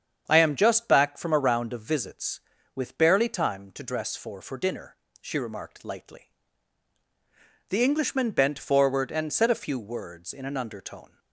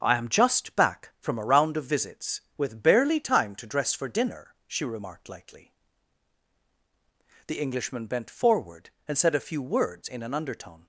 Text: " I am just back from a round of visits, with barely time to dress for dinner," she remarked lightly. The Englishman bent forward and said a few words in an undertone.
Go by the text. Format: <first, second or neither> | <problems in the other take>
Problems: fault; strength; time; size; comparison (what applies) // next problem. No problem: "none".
second | starts louder than the rest; strong; until 1.2 s; 8 dB; also in the second // says "for" twice; at 4.4 s